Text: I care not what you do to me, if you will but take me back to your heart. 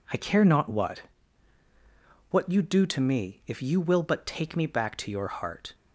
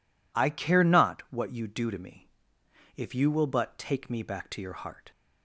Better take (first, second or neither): second